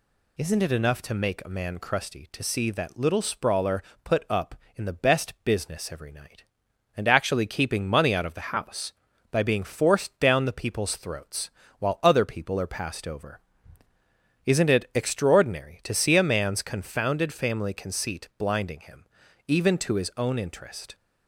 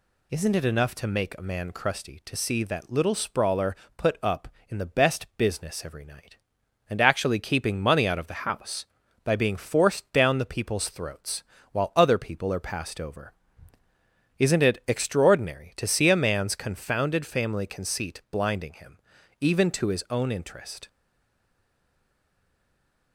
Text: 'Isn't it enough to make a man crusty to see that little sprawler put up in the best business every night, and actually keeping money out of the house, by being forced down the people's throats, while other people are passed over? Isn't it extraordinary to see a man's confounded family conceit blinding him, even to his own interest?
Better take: first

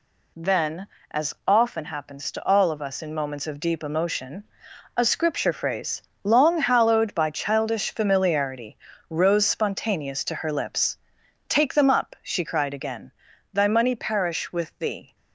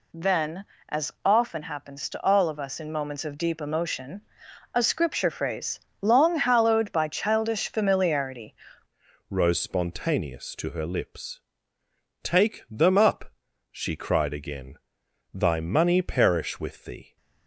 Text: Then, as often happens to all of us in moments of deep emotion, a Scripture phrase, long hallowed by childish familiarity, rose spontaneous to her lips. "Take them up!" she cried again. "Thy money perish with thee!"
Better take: first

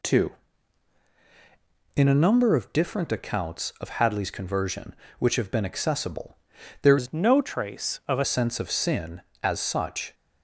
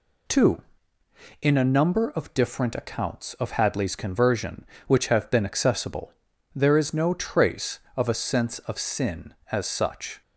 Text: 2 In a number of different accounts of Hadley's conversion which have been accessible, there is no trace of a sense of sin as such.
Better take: second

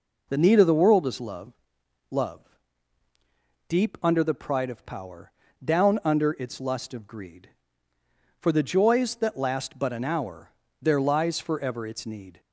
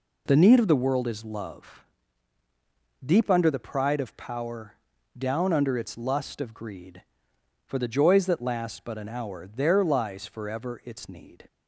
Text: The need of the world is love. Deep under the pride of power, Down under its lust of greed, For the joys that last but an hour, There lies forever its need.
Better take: second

